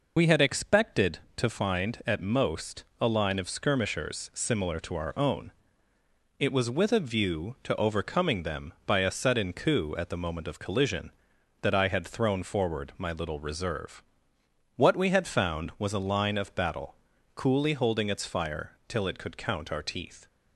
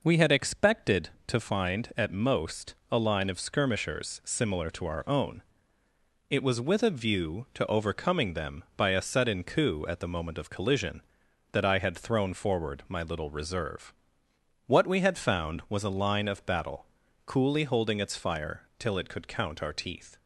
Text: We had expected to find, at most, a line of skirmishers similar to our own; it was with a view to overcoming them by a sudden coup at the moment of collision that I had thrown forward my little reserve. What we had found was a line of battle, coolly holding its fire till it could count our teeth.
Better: second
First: loses the start of "We"; at 0.1 s; 35 ms // pauses between "fire" and "till"; slight; at 18.7 s; 0.16 s long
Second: pauses between "fire" and "till"; slight; at 18.6 s; 0.16 s long

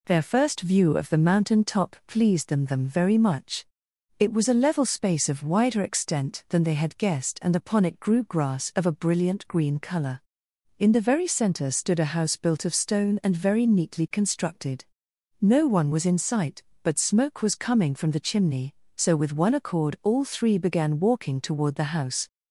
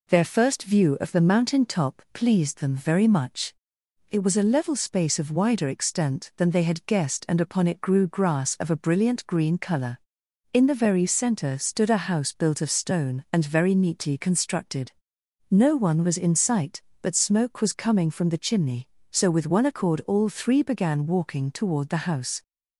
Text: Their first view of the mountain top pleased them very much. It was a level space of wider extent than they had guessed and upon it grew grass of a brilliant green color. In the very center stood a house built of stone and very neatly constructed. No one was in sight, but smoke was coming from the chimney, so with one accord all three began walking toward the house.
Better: second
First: says "them" twice; at 2.6 s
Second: none

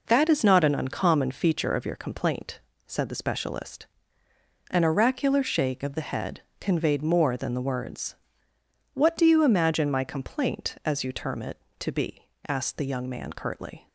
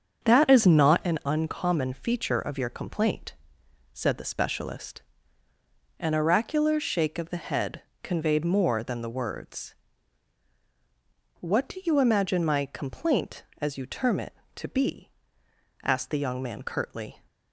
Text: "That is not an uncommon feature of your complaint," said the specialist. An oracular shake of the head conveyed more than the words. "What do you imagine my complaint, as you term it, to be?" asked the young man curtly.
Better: first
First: pauses between "head" and "conveyed"; slight; at 6.4 s; 0.18 s long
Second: starts louder than the rest; strong; until 1.1 s; 7 dB // pauses between "head" and "conveyed"; slight; at 7.8 s; 0.22 s long

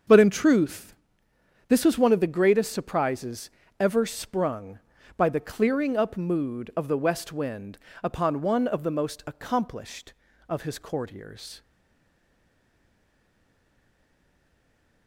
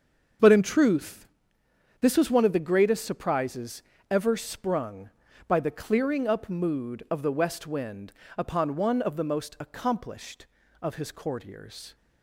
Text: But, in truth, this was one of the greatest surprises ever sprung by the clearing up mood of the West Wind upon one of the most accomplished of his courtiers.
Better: second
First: starts louder than the rest; until 1.8 s; 6.5 dB // pauses between "surprises" and "ever"; slight; at 3.5 s; 0.28 s long // pauses between "Wind" and "upon"; slight; at 7.7 s; 0.24 s long // stays silent after the last word; strong; from 11.6 s on; 3.4 s long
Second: starts louder than the rest; until 2.1 s; 6.5 dB // pauses between "surprises" and "ever"; slight; at 3.8 s; 0.26 s long // pauses between "Wind" and "upon"; slight; at 8.1 s; 0.24 s long

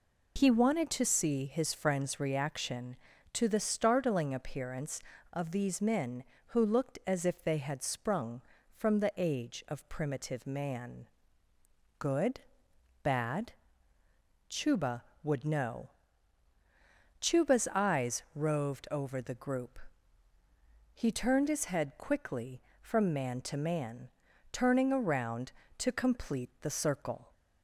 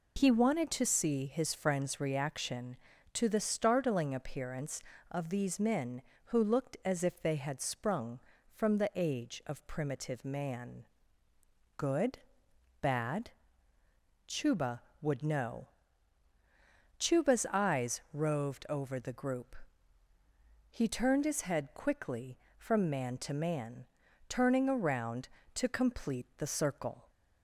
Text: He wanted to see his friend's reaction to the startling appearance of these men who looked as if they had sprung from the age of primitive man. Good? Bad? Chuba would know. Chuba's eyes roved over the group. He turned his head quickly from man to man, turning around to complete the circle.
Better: neither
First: none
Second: none

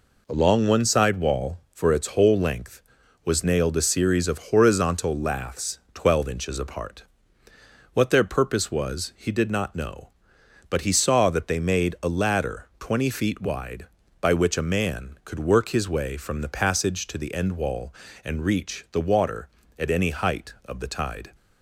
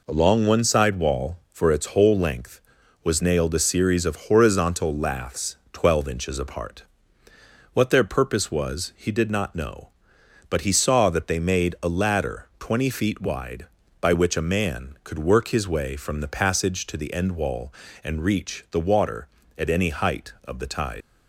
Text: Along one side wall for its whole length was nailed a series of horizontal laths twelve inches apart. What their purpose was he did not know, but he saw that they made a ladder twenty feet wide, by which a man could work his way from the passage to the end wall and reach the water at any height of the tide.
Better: first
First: none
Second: leaves "tide" unfinished; at 21.0 s; 135 ms

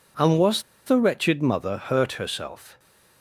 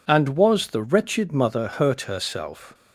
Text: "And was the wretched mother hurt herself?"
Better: second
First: pauses between "was" and "the"; slight; at 0.6 s; 0.24 s long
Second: none

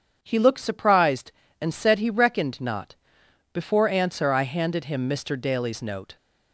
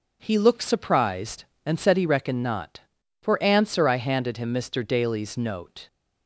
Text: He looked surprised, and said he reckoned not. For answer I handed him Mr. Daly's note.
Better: second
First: starts louder than the rest; strong; until 1.2 s; 7.5 dB // says "Before" for "For"; at 3.5 s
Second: none

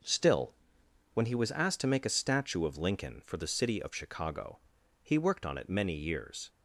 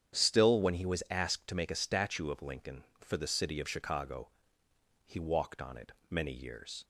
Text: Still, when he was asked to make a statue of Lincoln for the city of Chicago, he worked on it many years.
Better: first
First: none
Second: starts louder than the rest; strong; until 1.2 s; 9 dB // says "walked" for "worked"; at 5.1 s // pauses between "it" and "many"; slight; at 5.9 s; 0.16 s long

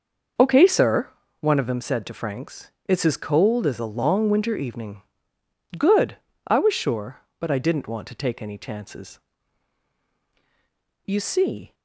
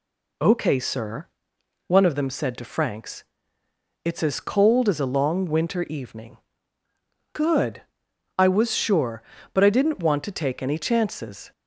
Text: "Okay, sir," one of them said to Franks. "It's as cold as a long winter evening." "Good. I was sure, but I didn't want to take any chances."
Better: second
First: starts louder than the rest; noticeable; until 1.6 s; 6 dB // goes on to say "You see"; noticeable; from 11.0 s on; 0.70 s long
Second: none

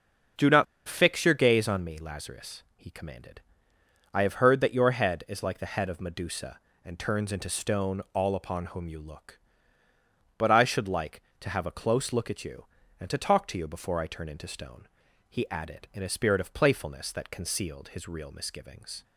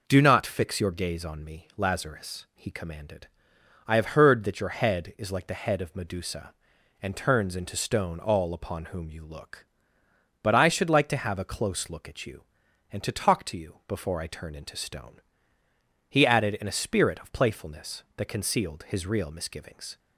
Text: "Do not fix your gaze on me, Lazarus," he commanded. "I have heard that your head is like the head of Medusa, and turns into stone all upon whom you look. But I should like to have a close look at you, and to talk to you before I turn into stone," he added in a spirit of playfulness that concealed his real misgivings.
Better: second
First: starts louder than the rest; until 1.6 s; 7 dB // pauses between "not" and "fix"; slight; at 0.6 s; 0.23 s long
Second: none

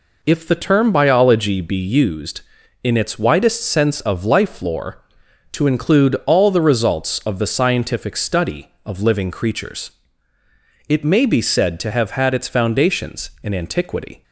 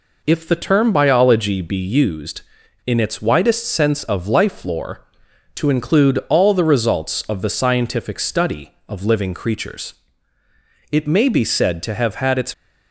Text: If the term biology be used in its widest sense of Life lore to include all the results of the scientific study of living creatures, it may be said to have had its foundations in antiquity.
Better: first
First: none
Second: stops before "foundations in antiquity"; at 12.5 s

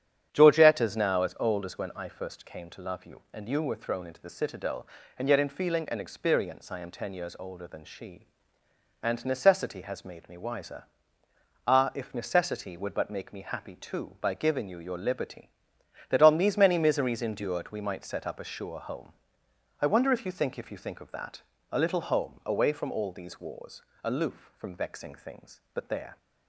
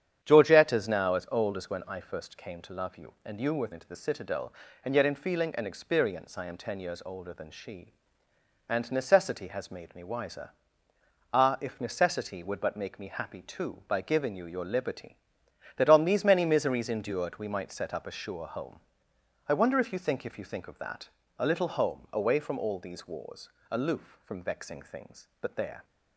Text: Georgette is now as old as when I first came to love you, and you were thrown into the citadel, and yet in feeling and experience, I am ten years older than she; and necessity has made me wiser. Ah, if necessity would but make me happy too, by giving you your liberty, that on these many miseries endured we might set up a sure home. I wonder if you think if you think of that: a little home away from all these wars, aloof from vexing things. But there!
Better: first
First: starts louder than the rest; strong; until 1.3 s; 9 dB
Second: starts louder than the rest; strong; until 1.2 s; 9 dB // skips "thrown"; at 3.7 s

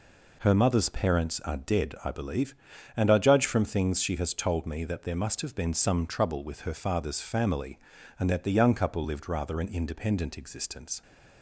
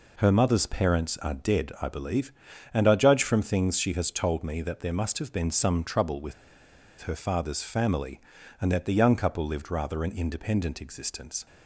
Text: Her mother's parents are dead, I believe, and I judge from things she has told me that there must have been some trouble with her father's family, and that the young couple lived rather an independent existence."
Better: first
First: none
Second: pauses between "with" and "her"; noticeable; at 6.3 s; 0.67 s long

